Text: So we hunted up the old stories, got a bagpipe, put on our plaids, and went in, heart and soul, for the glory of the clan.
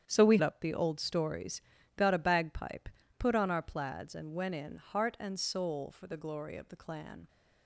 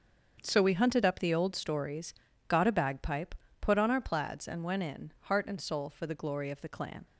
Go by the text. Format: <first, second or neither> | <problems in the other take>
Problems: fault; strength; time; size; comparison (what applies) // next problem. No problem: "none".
second | starts louder than the rest; strong; until 1.1 s; 8.5 dB; also in the second // skips "hunted"; at 0.3 s